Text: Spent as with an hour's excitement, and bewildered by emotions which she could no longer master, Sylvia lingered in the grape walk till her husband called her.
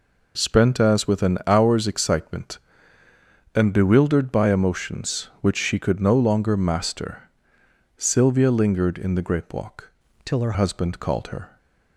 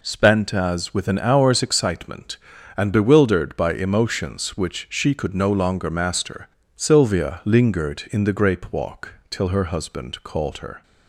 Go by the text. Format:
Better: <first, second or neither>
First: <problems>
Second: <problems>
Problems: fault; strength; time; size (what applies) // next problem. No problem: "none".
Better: second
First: changes voice from "till" to "her"; from 10.2 to 10.5 s; 0.3 s long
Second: none